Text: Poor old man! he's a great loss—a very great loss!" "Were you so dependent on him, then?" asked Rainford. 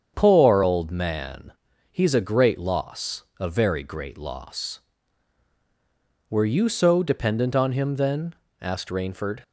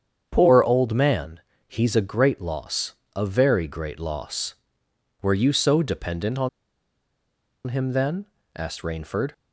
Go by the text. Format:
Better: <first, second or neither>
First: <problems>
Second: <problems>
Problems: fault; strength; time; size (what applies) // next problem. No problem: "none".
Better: first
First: starts louder than the rest; strong; until 1.1 s; 7.5 dB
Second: starts louder than the rest; strong; until 1.3 s; 8 dB // pauses between "on" and "him"; at 6.4 s; 1.1 s long